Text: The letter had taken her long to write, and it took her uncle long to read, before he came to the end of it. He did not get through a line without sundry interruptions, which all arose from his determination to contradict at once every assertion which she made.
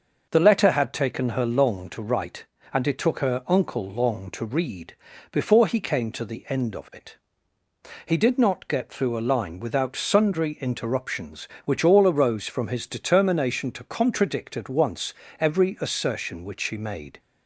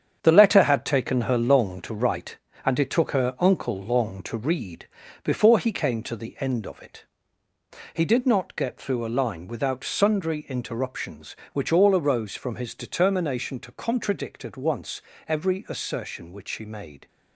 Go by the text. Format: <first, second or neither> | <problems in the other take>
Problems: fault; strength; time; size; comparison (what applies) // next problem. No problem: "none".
first | gets quieter; strong; throughout; 7.5 dB // starts louder than the rest; strong; until 1.2 s; 8 dB; noticeable in the first // pauses between "once" and "every"; slight; at 15.0 s; 0.28 s long; slight in the first